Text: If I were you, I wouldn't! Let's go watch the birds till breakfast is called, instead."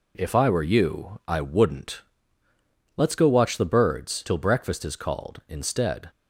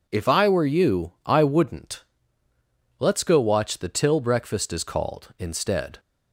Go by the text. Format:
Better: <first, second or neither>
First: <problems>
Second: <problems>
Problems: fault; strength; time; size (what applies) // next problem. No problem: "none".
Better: first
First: none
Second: skips "birds"; at 3.8 s